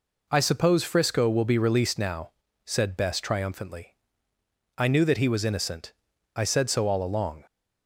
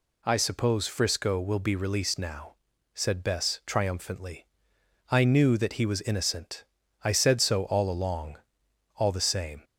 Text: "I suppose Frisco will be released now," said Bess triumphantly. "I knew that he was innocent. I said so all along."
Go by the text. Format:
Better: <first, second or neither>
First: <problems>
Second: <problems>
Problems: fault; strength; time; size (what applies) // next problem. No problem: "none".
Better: first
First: none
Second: goes on to say "All the same"; noticeable; from 8.9 s on; 0.68 s long